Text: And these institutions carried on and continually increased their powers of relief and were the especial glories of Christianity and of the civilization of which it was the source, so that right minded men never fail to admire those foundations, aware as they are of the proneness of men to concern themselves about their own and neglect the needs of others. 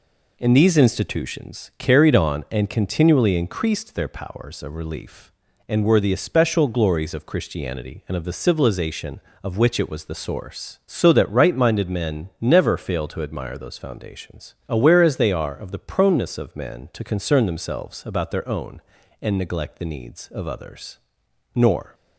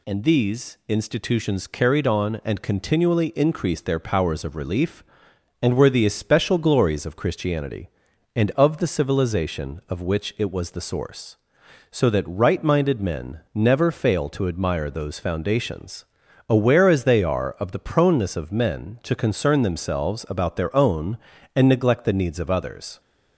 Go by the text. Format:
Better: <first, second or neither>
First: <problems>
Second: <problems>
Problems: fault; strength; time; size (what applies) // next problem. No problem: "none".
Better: second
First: goes on to say "Nor"; slight; from 21.5 s on; 0.40 s long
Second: none